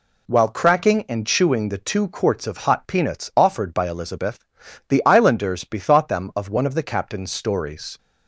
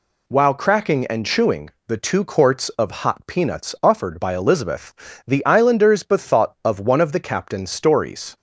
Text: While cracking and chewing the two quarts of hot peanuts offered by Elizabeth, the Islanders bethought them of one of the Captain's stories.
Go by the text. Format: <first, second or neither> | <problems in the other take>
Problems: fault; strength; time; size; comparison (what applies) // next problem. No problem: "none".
first | pauses between "chewing" and "the"; slight; at 1.7 s; 0.16 s long // skips "them"; at 6.5 s